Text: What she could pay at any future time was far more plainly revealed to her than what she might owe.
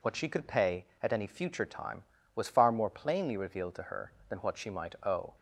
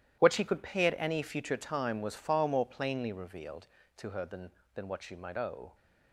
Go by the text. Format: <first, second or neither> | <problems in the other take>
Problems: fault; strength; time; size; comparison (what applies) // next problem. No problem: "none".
first | starts louder than the rest; strong; until 1.2 s; 12.5 dB // says "than" twice; at 4.7 s